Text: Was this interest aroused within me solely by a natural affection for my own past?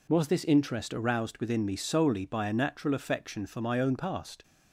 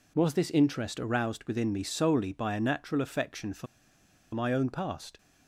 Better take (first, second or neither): first